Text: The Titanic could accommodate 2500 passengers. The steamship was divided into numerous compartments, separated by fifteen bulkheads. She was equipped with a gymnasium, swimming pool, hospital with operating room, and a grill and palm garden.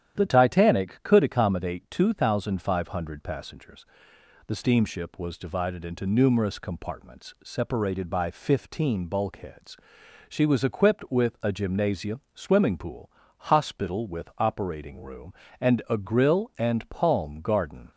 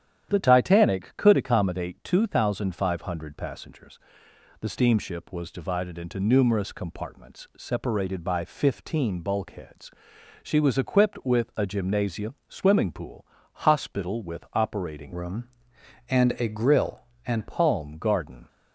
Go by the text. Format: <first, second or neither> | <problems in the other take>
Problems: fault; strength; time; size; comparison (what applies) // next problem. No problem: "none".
first | starts louder than the rest; strong; until 1.3 s; 10 dB; strong in the first // changes voice from "room" to "and"; from 15.1 to 17.4 s; 2.3 s long